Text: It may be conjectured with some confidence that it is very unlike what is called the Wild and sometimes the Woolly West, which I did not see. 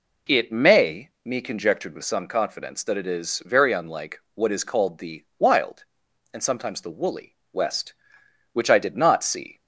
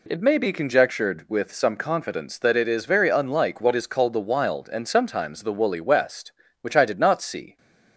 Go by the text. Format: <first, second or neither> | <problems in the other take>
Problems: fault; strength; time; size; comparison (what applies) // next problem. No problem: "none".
second | says "me" for "be"; at 1.2 s // pauses between "unlike" and "what"; slight; at 4.1 s; 0.16 s long // pauses between "the" and "Wild"; slight; at 5.2 s; 0.16 s long // pauses between "Woolly" and "West"; slight; at 7.3 s; 0.18 s long